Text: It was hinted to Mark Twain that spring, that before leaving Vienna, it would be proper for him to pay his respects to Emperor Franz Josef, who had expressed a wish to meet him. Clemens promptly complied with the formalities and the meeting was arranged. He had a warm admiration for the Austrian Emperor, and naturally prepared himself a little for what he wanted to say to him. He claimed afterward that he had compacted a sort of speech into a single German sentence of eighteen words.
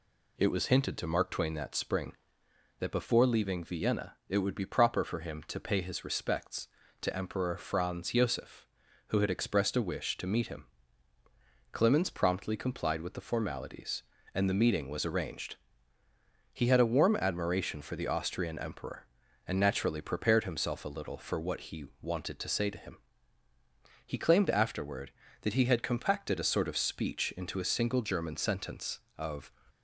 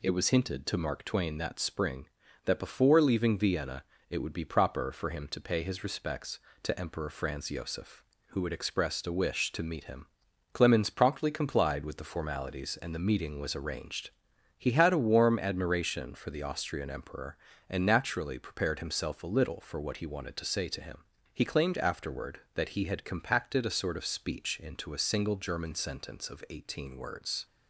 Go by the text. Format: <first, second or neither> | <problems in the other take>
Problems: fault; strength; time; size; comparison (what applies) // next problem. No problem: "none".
second | pauses between "he" and "wanted"; slight; at 21.8 s; 0.18 s long // stops before "eighteen words"; at 29.6 s